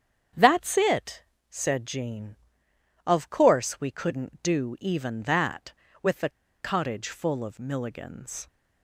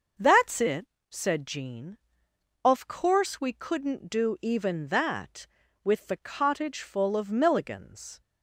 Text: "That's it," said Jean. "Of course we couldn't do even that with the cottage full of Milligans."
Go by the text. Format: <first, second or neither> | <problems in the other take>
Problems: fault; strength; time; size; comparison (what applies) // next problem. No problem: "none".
second | starts louder than the rest; strong; until 1.6 s; 8 dB; noticeable in the second // pauses between "the" and "cottage"; slight; at 6.2 s; 0.31 s long